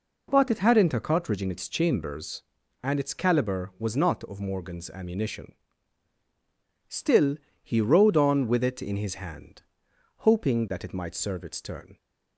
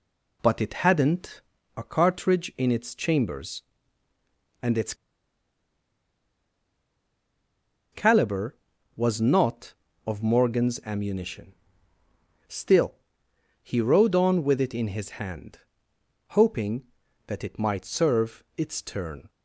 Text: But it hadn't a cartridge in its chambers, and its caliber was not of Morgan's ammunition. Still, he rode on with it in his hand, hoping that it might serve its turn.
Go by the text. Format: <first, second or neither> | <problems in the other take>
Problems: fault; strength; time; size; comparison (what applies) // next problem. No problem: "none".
first | pauses between "hadn't" and "a"; slight; at 1.4 s; 0.34 s long // pauses between "its" and "caliber"; strong; at 4.9 s; 2.9 s long